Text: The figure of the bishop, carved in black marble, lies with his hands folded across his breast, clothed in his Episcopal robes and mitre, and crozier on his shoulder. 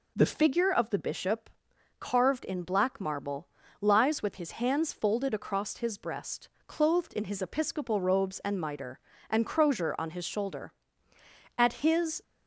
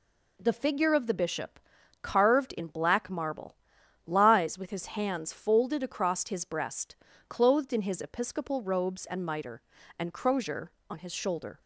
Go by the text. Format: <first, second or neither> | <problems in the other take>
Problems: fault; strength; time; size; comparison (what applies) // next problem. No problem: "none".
second | goes on to say "At his"; noticeable; from 11.5 s on; 0.66 s long